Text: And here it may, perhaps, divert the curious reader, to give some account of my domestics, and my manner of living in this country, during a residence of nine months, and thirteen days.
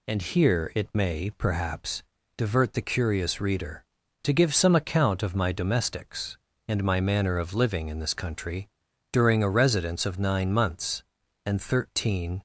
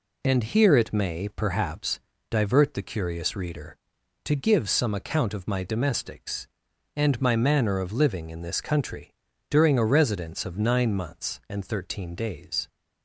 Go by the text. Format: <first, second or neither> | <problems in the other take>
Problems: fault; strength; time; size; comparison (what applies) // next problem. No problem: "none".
second | stops before "days"; at 12.3 s